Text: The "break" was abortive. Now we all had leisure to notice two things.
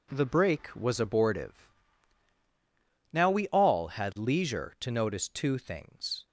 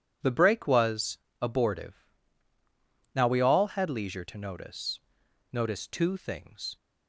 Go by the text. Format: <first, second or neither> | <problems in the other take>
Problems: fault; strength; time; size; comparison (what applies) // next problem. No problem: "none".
first | pauses between "was" and "abortive"; slight; at 1.1 s; 0.24 s long // says "notice" twice; at 5.5 s